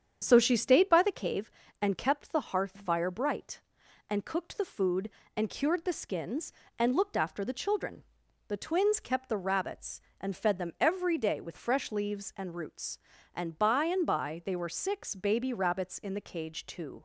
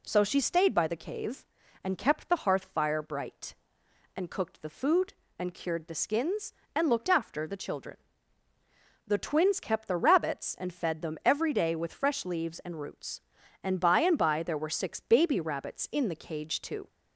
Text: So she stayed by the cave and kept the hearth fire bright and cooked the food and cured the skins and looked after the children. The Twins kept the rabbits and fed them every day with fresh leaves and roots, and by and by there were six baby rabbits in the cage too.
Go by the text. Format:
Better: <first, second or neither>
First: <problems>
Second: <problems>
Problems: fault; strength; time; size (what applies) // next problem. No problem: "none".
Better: second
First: starts louder than the rest; strong; until 1.2 s; 8 dB // says "they" for "there"; at 14.4 s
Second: none